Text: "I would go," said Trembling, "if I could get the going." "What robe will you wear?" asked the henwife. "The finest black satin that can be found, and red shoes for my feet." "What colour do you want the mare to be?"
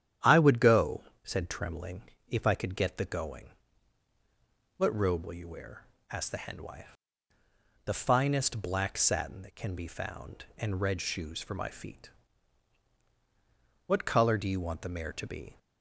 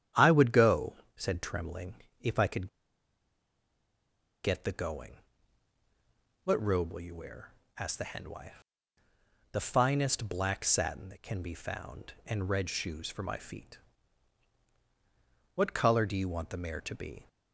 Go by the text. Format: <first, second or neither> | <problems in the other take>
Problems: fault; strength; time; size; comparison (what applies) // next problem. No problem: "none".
first | starts louder than the rest; strong; until 1.3 s; 10 dB; strong in the first // pauses between "could" and "get"; strong; at 2.6 s; 1.7 s long